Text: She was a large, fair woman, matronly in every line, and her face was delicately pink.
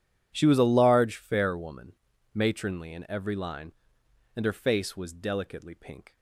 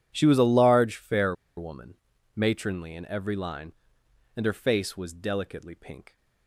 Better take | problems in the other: first | pauses between "fair" and "woman"; slight; at 1.3 s; 0.22 s long

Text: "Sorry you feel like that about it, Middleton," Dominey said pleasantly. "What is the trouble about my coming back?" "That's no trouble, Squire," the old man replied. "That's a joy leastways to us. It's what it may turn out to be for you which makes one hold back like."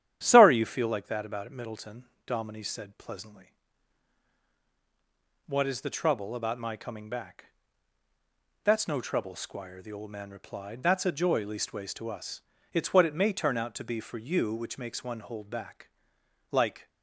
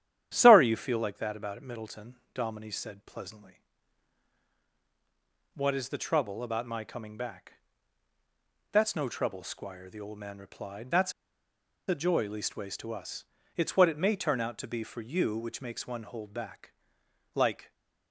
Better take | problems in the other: first | starts louder than the rest; strong; until 1.3 s; 10.5 dB; strong in the first // pauses between "That's" and "a"; noticeable; at 11.1 s; 0.75 s long // pauses between "back" and "like"; noticeable; at 16.7 s; 0.60 s long; noticeable in the first

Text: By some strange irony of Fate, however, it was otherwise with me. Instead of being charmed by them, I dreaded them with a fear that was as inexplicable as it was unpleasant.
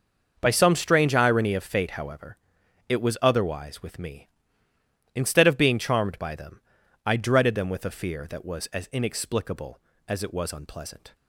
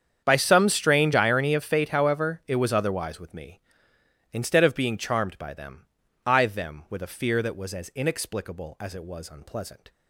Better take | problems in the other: first | starts louder than the rest; strong; until 1.2 s; 8 dB; also in the first // skips "dreaded"; at 6.4 s

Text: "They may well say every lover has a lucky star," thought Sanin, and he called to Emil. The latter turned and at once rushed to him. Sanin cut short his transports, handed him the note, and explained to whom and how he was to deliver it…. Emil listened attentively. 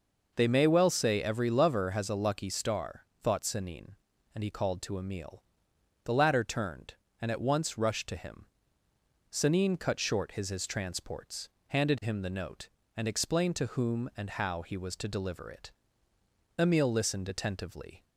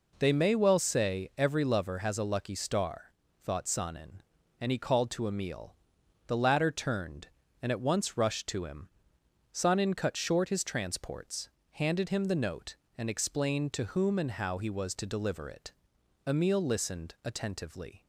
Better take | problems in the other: second | says "his" twice; at 10.4 s

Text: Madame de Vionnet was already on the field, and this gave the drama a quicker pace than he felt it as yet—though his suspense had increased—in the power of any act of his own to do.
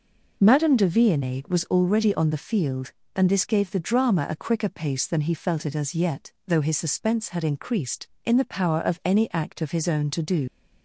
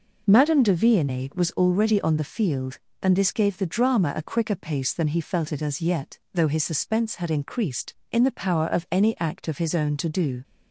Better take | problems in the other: second | leaves "do" unfinished; at 10.4 s; 85 ms

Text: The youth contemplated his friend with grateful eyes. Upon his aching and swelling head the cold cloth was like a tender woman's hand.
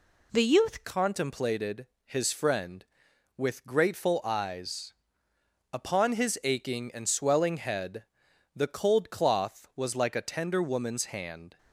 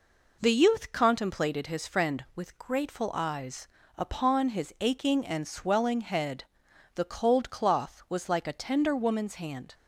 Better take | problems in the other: second | changes voice at "contemplated"; from 0.8 s on; 10.7 s long // pauses between "contemplated" and "his"; slight; at 1.8 s; 0.20 s long // pauses between "head" and "the"; noticeable; at 8.0 s; 0.50 s long; noticeable in the second

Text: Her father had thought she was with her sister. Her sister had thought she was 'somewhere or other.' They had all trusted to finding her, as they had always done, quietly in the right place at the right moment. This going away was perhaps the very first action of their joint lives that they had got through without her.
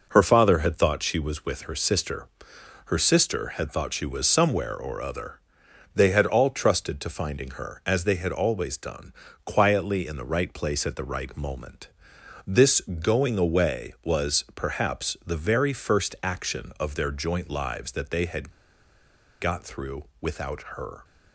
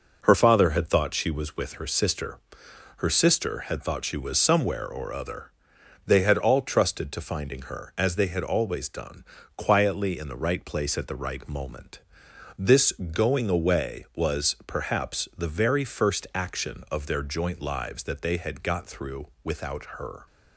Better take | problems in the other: second | pauses between "had" and "got"; noticeable; at 18.5 s; 0.90 s long

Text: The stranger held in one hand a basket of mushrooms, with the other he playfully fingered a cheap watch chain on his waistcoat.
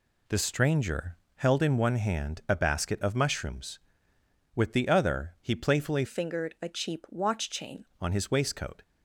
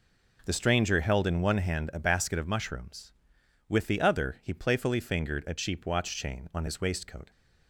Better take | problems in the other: second | pauses between "stranger" and "held"; slight; at 1.1 s; 0.18 s long // changes voice from "fingered" to "chain"; from 6.0 to 7.8 s; 1.8 s long

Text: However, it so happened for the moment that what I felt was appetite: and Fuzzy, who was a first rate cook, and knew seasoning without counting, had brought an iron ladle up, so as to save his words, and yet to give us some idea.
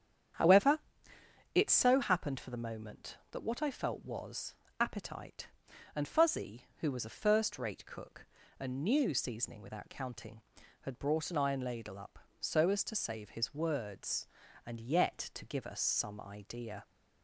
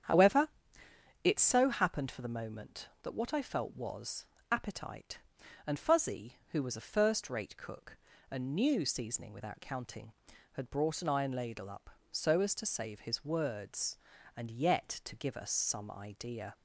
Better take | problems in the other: neither | starts louder than the rest; strong; the same in both // pauses between "was" and "appetite"; slight; the same in both

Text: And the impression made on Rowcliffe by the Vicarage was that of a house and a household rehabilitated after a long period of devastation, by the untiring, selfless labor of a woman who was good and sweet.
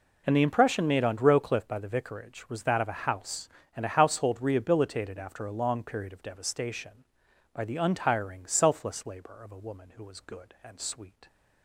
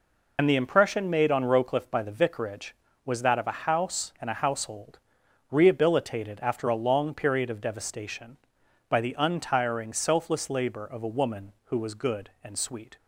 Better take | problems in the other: first | loses the start of "And"; at 0.3 s; 50 ms // pauses between "household" and "rehabilitated"; noticeable; at 4.9 s; 0.52 s long

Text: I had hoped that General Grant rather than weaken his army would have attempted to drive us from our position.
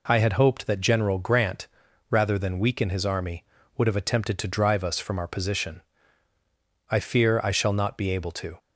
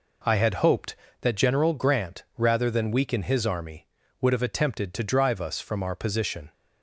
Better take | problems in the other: second | pauses between "Grant" and "rather"; at 1.6 s; 0.44 s long; slight in the second // goes on to say "I fear I shall not be able to"; strong; from 6.8 s on; 1.7 s long

